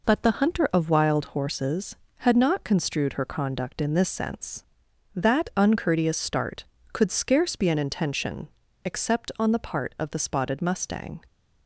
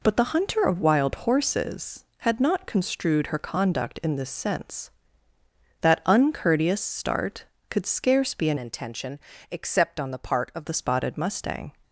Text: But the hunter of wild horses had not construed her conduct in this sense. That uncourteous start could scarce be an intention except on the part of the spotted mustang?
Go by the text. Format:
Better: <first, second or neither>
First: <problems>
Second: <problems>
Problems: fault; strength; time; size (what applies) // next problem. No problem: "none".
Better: first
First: pauses between "intention" and "except"; slight; at 8.4 s; 0.36 s long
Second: changes voice from "intention" to "of"; from 8.5 to 10.6 s; 2.1 s long // pauses between "intention" and "except"; slight; at 9.1 s; 0.32 s long